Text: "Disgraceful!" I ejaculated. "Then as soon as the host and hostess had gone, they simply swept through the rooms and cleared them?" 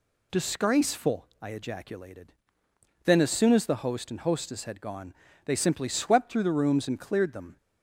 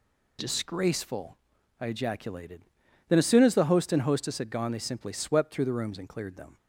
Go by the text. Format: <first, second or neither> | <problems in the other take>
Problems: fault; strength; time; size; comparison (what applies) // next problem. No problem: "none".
neither | none